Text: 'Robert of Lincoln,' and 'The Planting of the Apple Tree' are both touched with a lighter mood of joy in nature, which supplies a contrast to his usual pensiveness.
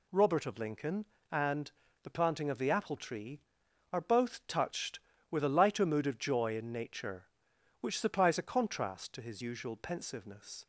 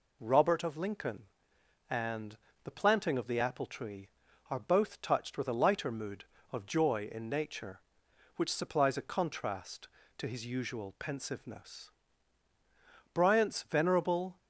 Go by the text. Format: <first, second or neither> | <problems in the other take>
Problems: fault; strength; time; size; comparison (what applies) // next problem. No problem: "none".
first | pauses between "and" and "The"; slight; at 2.3 s; 0.26 s long; slight in the first // goes on to say "Bryant's venerable"; noticeable; from 13.1 s on; 1.2 s long